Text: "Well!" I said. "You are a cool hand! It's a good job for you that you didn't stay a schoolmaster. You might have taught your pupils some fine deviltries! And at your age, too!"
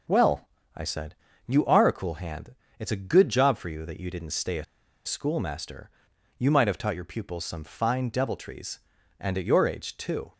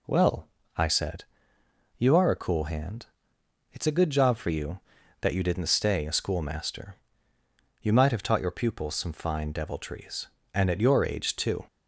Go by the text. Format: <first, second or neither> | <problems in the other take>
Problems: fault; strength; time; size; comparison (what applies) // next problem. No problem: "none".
second | pauses between "a" and "schoolmaster"; at 4.6 s; 0.41 s long